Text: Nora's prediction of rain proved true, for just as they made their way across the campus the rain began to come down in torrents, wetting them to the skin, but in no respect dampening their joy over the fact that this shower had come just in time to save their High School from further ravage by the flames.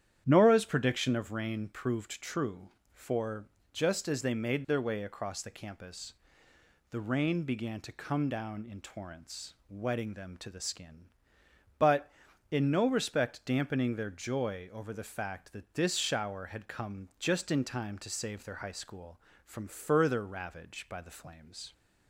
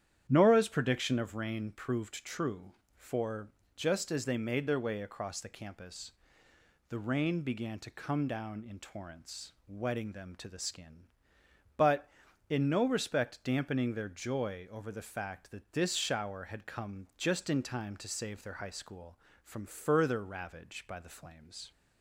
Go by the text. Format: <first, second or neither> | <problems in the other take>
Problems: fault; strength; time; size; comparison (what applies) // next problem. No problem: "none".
neither | starts louder than the rest; strong; the same in both // pauses between "for" and "just"; slight; the same in both // pauses between "campus" and "the"; noticeable; the same in both